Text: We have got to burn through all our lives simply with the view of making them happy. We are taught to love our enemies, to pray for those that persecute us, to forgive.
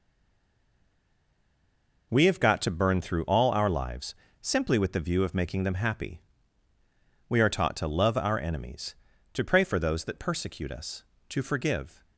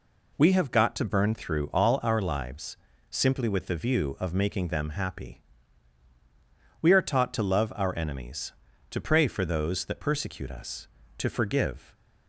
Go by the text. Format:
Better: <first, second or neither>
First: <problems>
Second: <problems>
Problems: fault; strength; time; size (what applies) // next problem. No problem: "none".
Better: second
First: stays silent before the first word; noticeable; until 2.1 s; 2.1 s long // pauses between "lives" and "simply"; slight; at 4.1 s; 0.26 s long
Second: pauses between "lives" and "simply"; slight; at 2.7 s; 0.36 s long